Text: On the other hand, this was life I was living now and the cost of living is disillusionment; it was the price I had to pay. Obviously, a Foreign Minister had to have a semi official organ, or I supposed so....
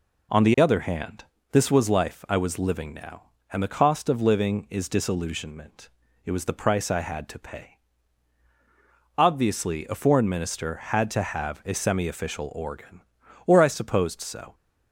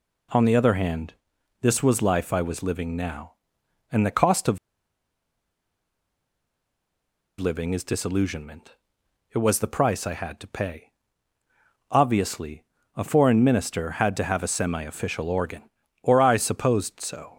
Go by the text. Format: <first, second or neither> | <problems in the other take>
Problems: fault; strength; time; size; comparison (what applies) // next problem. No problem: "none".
first | pauses between "of" and "living"; strong; at 4.5 s; 2.8 s long